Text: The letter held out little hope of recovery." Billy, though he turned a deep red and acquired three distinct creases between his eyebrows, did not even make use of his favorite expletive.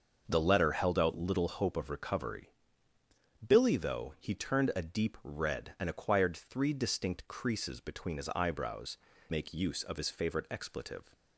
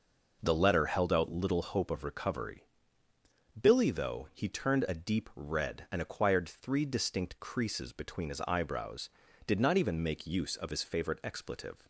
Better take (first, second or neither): second